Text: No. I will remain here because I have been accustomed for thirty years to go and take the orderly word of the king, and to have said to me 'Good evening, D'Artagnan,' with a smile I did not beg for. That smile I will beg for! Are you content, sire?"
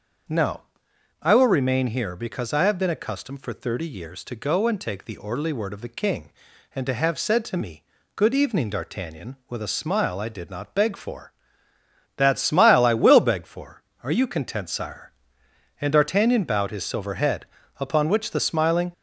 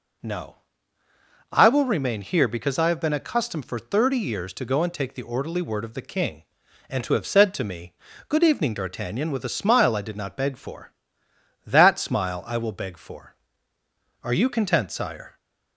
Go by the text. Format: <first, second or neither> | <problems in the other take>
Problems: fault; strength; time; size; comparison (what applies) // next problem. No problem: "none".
second | starts louder than the rest; until 1.8 s; 6.5 dB // pauses between "me" and "Good"; slight; at 7.8 s; 0.32 s long; slight in the second // goes on to say "And D'Artagnan bowed his silver head upon which the smiling"; strong; from 15.8 s on; 3.1 s long